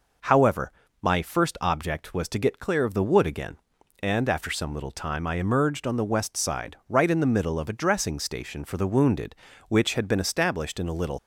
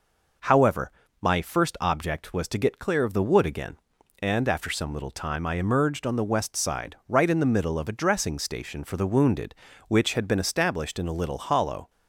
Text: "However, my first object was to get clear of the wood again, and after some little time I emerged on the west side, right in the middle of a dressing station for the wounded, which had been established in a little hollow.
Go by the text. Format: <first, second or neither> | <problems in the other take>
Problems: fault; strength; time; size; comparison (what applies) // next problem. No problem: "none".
second | stops before "hollow"; at 11.1 s